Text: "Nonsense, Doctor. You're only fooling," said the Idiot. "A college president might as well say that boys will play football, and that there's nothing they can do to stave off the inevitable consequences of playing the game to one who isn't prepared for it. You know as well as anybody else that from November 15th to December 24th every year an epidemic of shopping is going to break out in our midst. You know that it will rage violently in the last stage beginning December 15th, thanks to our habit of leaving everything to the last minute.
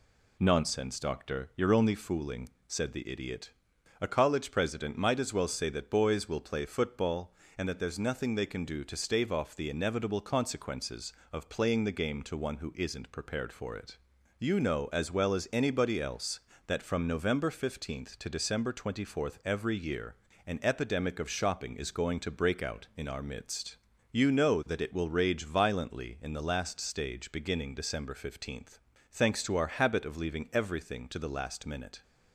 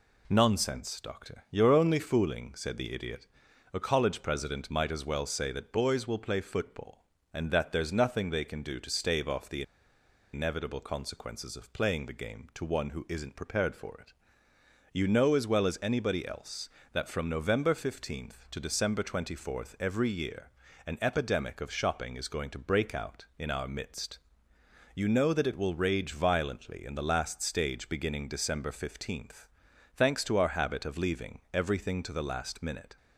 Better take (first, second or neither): first